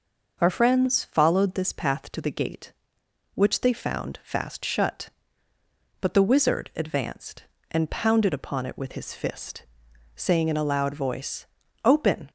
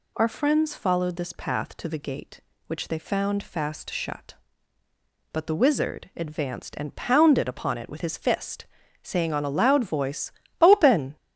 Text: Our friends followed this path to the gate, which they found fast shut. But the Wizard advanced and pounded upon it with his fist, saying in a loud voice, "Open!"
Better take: first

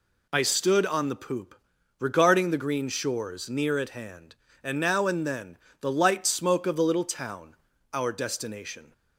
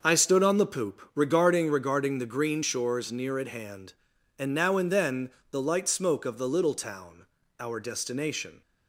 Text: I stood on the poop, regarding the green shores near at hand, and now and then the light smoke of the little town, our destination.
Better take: first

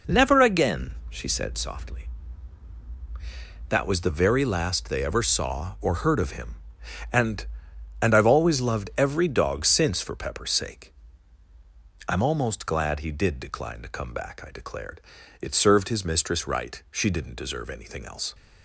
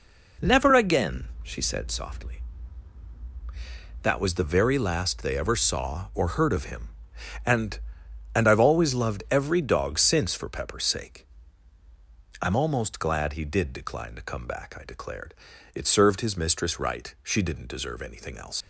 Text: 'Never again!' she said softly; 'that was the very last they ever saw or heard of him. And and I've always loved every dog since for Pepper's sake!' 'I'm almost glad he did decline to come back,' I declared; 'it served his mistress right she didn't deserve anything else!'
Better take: first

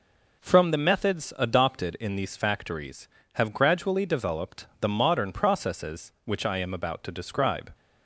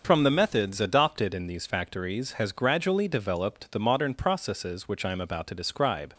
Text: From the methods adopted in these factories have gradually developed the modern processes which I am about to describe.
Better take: first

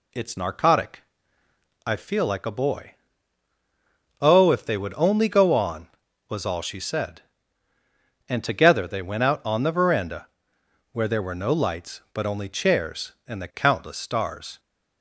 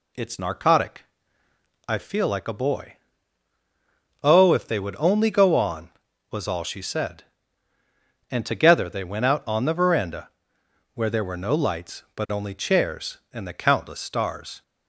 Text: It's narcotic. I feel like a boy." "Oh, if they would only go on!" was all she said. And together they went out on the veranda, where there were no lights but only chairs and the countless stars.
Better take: neither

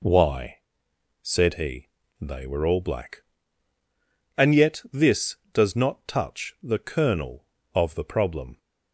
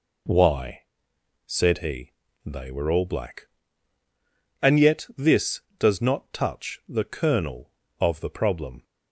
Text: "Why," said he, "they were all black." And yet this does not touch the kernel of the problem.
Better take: neither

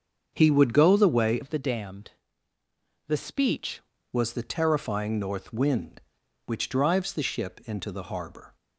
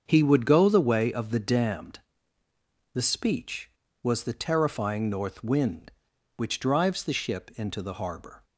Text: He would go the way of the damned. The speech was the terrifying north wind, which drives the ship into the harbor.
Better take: second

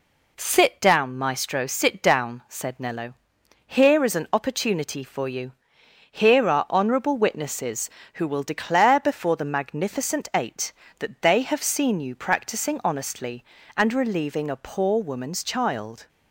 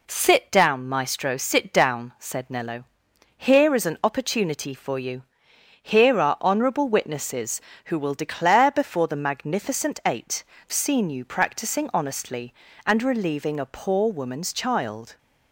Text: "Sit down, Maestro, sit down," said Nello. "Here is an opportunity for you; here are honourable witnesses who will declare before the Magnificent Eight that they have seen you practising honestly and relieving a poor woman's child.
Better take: first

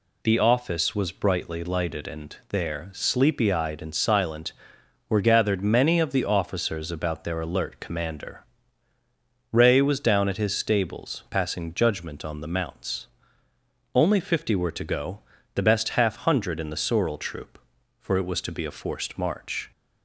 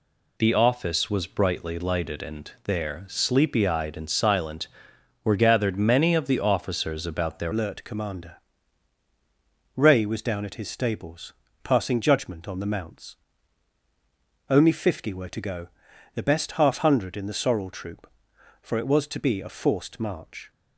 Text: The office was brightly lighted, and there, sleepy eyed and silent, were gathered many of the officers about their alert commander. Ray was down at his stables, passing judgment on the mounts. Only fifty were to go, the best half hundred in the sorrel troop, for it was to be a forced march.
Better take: first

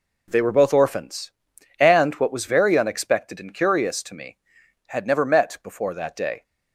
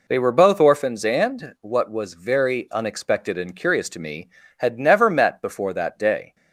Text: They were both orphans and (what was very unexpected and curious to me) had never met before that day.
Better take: neither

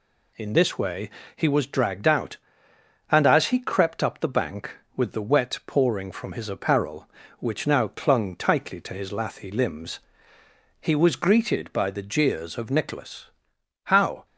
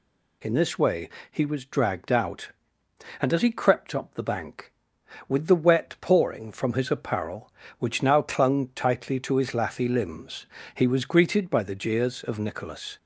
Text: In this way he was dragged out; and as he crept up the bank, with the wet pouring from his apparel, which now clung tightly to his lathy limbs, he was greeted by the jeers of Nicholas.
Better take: second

